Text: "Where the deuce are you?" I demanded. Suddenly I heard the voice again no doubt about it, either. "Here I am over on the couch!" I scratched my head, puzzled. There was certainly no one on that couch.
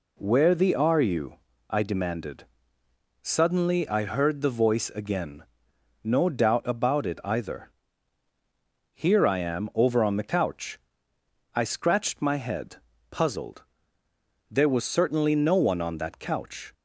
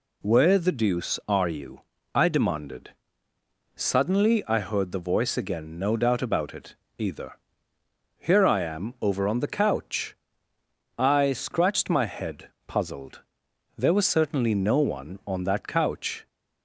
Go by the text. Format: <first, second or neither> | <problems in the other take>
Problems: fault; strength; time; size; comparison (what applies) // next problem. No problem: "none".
second | skips "deuce"; at 0.7 s // pauses between "again" and "no"; noticeable; at 5.4 s; 0.60 s long